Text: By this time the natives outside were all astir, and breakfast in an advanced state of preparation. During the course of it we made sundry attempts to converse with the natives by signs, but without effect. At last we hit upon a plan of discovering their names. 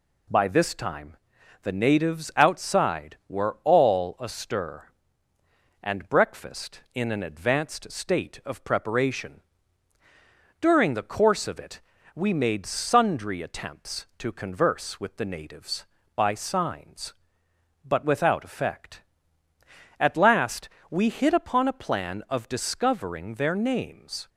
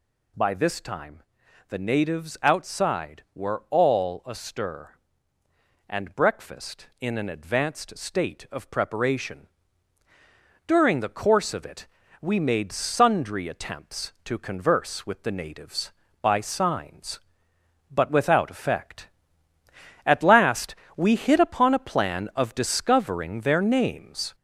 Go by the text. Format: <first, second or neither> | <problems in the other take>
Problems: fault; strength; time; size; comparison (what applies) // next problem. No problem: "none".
first | gets louder; throughout; 3.5 dB // pauses between "time" and "the"; noticeable; at 1.2 s; 0.46 s long; noticeable in the first // pauses between "it" and "we"; slight; at 11.8 s; 0.34 s long; slight in the first // pauses between "last" and "we"; slight; at 20.7 s; 0.22 s long; slight in the first